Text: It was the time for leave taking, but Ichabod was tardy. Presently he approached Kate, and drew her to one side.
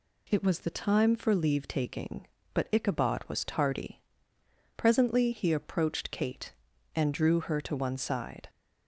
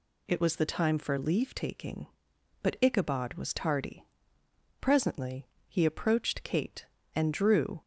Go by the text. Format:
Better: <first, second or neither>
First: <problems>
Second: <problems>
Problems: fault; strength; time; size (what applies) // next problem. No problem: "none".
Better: first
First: none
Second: pauses between "Presently" and "he"; slight; at 5.4 s; 0.20 s long // stops before "her to one side"; at 7.8 s